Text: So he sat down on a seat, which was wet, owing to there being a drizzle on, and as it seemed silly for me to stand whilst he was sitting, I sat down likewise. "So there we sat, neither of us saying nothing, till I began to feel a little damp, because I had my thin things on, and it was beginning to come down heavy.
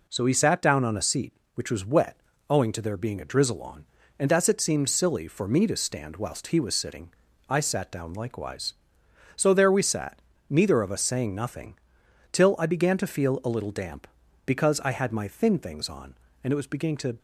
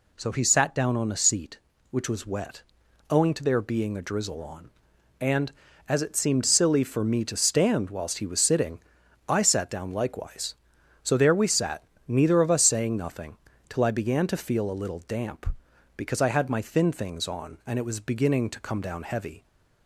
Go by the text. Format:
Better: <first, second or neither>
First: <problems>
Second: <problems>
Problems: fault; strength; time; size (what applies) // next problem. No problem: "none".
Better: second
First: stops before "come down heavy"; at 17.1 s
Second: none